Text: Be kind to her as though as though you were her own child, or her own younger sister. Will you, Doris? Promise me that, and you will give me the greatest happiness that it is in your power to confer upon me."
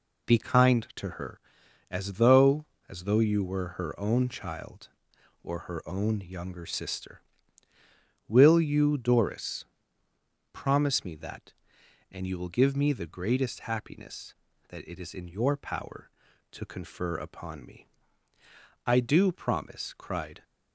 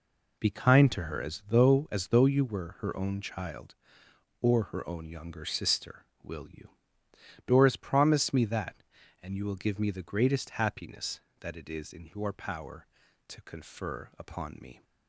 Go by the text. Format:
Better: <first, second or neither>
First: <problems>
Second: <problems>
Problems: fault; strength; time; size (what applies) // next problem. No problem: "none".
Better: second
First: goes on to say "I do promise cried"; from 18.8 s on; 1.5 s long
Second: none